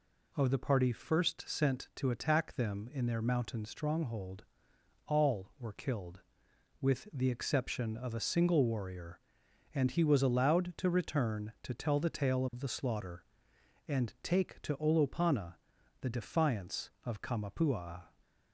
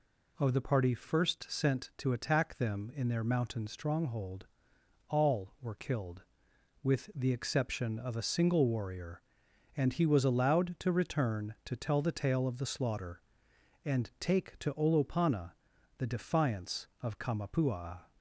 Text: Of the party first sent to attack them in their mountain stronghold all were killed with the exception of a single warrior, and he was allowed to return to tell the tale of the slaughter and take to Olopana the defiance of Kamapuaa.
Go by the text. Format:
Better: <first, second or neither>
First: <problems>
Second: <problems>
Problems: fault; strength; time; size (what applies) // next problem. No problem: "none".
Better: neither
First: pauses between "stronghold" and "all"; noticeable; at 4.4 s; 0.62 s long // pauses between "Olopana" and "the"; noticeable; at 15.5 s; 0.46 s long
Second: pauses between "stronghold" and "all"; noticeable; at 4.4 s; 0.62 s long // pauses between "Olopana" and "the"; noticeable; at 15.5 s; 0.46 s long